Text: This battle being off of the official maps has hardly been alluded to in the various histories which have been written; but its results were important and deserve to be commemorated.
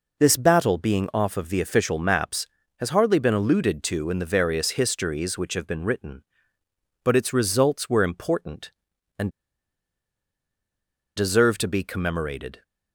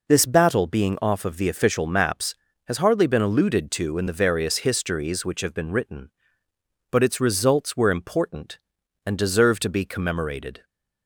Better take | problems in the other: second | pauses between "and" and "deserve"; strong; at 9.2 s; 1.8 s long

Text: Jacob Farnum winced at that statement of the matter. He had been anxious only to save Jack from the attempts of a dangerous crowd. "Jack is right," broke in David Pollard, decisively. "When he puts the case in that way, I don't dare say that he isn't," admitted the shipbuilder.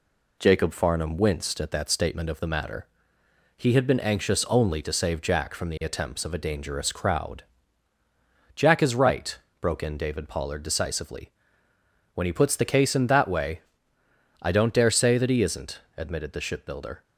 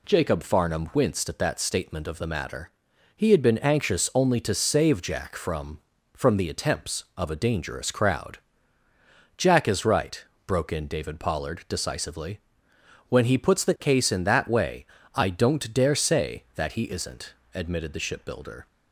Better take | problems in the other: first | says "from" twice; at 6.1 s

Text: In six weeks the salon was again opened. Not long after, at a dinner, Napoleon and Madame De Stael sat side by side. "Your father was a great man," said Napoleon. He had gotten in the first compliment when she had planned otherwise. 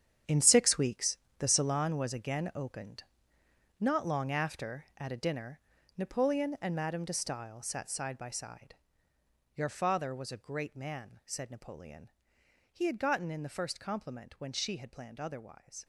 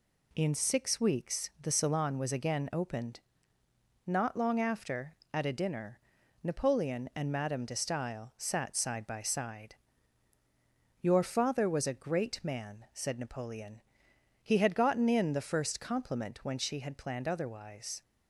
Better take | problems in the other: second | gets quieter; strong; throughout; 12 dB // pauses between "weeks" and "the"; slight; at 1.1 s; 0.18 s long

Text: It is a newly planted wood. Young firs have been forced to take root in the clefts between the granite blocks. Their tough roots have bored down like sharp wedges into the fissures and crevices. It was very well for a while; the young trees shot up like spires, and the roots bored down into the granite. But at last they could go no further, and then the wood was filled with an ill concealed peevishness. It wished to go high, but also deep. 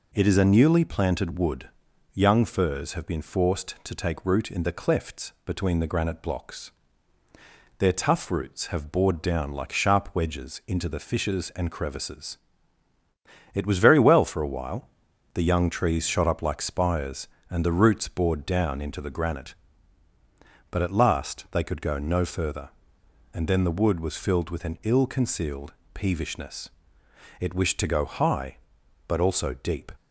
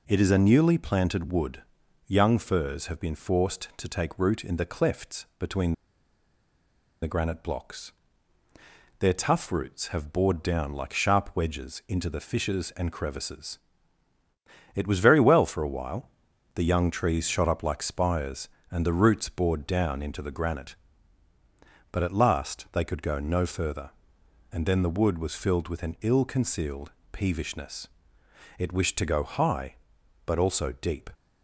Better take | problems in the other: first | pauses between "between" and "the"; strong; at 5.7 s; 1.3 s long // pauses between "concealed" and "peevishness"; slight; at 26.9 s; 0.20 s long; slight in the first

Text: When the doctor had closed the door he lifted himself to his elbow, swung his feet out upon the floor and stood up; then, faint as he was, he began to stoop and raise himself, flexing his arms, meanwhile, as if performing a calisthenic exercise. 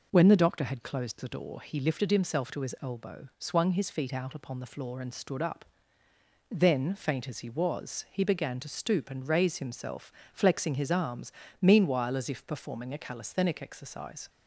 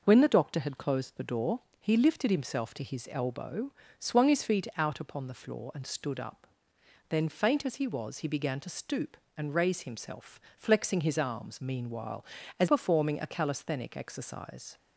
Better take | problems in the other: first | pauses between "door" and "he"; slight; at 1.5 s; 0.20 s long // skips "if"; at 12.6 s

